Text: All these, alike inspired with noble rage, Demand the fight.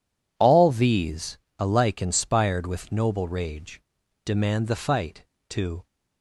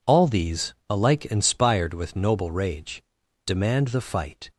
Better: second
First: goes on to say "To"; slight; from 5.5 s on; 0.36 s long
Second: none

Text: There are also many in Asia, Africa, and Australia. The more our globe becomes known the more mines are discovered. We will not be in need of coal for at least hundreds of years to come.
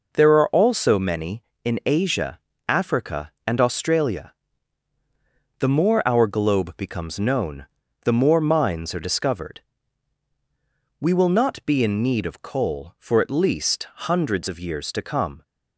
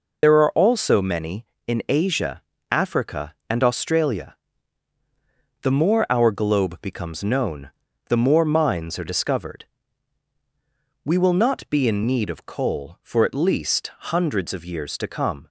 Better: first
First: pauses between "known" and "the"; at 7.6 s; 0.38 s long // pauses between "least" and "hundreds"; slight; at 13.8 s; 0.22 s long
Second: loses the start of "There"; at 0.2 s; 65 ms // pauses between "known" and "the"; at 7.7 s; 0.38 s long // pauses between "least" and "hundreds"; slight; at 13.8 s; 0.22 s long

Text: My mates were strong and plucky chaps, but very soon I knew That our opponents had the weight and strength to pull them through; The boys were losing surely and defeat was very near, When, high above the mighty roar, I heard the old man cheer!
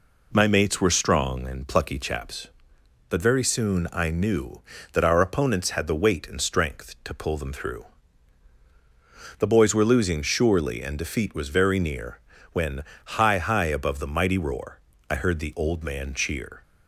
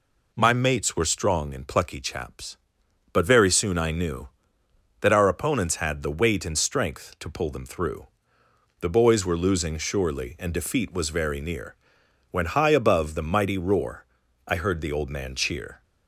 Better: second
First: says "high" twice; at 13.4 s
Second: none

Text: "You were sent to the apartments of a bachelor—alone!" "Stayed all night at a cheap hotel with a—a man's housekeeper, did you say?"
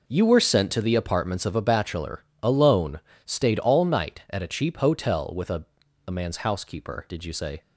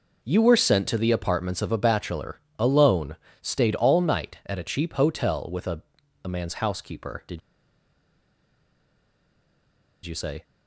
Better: first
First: none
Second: pauses between "did" and "you"; strong; at 7.4 s; 2.6 s long

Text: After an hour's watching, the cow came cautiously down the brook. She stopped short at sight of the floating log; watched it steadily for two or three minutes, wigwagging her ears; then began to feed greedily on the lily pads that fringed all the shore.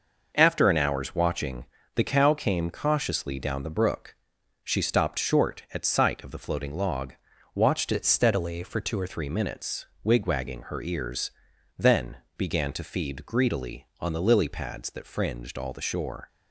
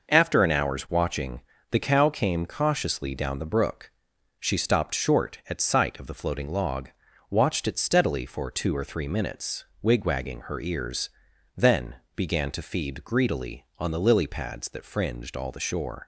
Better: second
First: changes voice from "it" to "or"; from 7.9 to 9.0 s; 1.1 s long // pauses between "then" and "began"; slight; at 12.1 s; 0.20 s long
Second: pauses between "then" and "began"; slight; at 11.9 s; 0.20 s long

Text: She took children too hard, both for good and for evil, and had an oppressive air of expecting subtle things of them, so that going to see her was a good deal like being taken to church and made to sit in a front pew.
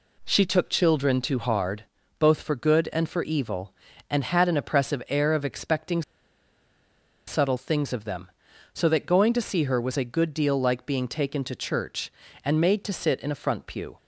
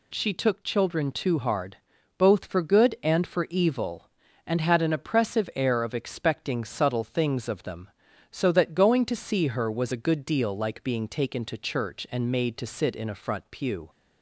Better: second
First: pauses between "expecting" and "subtle"; strong; at 6.0 s; 1.2 s long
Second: none

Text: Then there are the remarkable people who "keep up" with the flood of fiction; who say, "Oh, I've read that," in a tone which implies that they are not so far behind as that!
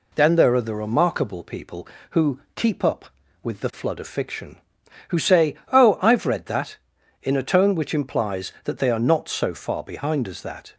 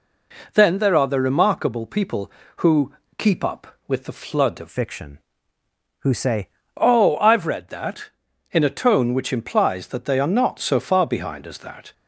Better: first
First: pauses between "who" and "keep"; slight; at 2.3 s; 0.16 s long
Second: pauses between "who" and "keep"; slight; at 2.9 s; 0.26 s long // changes voice from "fiction" to "say"; from 4.6 to 6.4 s; 1.8 s long

